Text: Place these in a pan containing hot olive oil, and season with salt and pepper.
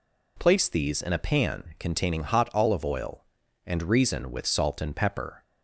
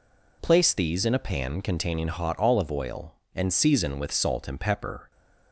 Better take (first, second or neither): second